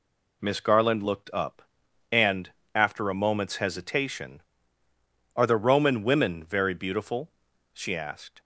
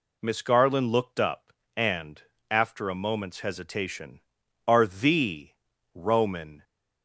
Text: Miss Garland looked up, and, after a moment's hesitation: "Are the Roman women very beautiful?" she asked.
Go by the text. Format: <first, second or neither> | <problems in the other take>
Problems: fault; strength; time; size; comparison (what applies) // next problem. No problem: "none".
first | pauses between "the" and "Roman"; at 5.5 s; 0.42 s long // stops before "women very beautiful she asked"; at 6.6 s